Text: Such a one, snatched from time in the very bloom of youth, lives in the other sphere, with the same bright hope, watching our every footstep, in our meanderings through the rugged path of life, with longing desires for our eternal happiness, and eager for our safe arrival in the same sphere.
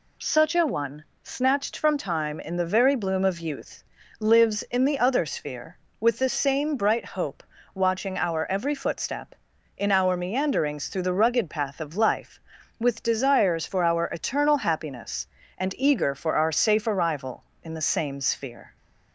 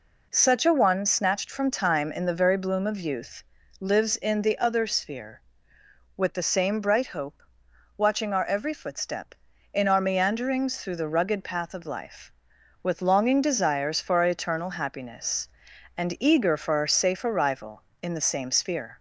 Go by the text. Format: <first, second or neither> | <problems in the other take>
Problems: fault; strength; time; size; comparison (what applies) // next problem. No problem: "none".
second | skips "longing"; at 13.0 s